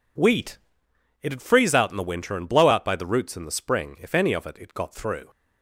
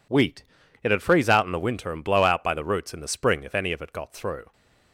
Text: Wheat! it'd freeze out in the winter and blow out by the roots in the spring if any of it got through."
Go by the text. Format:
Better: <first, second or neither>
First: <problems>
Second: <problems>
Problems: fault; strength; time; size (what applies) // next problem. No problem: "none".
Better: second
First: says "it" twice; at 4.5 s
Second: none